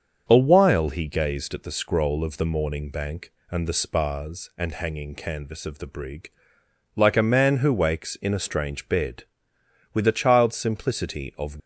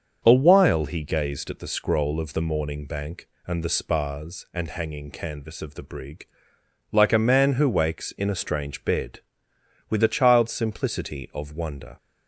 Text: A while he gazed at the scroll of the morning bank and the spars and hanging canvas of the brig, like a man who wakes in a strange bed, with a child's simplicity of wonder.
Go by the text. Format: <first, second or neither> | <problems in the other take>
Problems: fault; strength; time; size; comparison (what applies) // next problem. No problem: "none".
second | starts louder than the rest; until 1.2 s; 7 dB; also in the second // stops before "wonder"; at 11.5 s